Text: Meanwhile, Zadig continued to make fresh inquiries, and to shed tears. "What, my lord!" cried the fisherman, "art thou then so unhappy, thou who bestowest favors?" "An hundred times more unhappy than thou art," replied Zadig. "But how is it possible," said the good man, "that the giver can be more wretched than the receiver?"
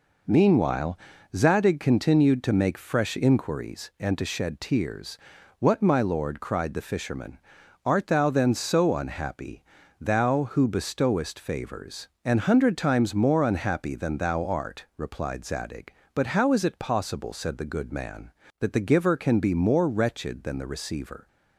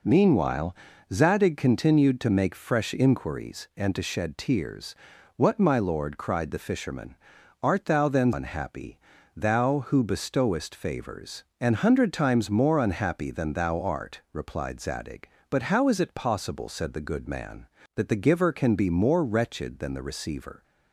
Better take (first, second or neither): first